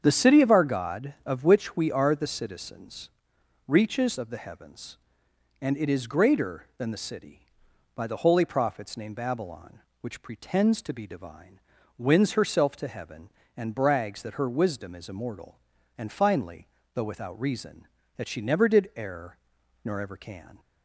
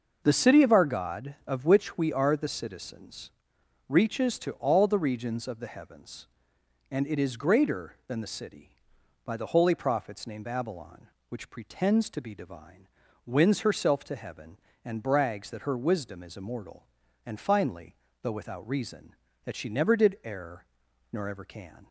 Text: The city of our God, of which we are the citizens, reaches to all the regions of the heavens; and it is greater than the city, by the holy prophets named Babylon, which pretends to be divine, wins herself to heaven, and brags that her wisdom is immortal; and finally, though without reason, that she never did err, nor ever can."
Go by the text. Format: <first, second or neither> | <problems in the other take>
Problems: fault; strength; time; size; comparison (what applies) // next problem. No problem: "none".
second | starts louder than the rest; strong; until 1.0 s; 7.5 dB // skips "to all the regions"; at 4.1 s